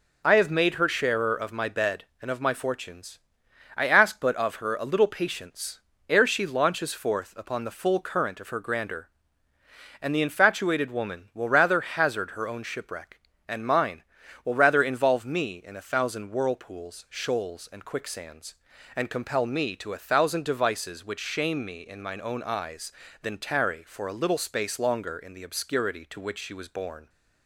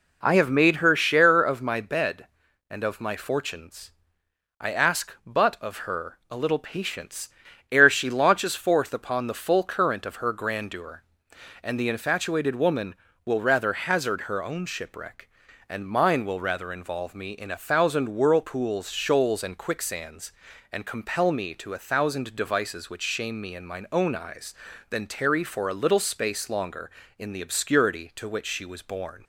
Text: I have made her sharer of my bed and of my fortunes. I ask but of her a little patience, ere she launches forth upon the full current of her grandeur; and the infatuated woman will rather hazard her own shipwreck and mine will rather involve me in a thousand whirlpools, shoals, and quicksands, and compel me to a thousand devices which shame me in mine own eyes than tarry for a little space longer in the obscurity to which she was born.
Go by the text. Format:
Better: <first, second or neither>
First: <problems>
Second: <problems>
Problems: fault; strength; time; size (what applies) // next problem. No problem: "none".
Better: neither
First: none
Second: none